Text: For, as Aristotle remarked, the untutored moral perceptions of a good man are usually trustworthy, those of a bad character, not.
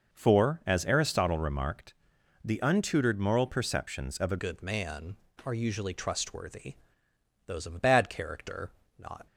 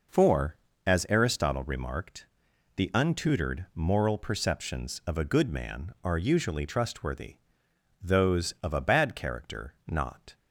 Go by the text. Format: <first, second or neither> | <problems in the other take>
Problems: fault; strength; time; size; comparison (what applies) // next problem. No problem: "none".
second | changes voice at "good"; from 4.3 s on; 4.9 s long